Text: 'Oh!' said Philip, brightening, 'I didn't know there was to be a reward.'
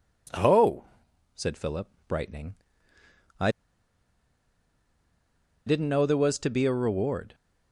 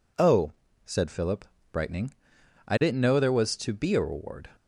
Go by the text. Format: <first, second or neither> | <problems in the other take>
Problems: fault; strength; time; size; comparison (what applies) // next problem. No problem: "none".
second | pauses between "I" and "didn't"; strong; at 3.4 s; 2.1 s long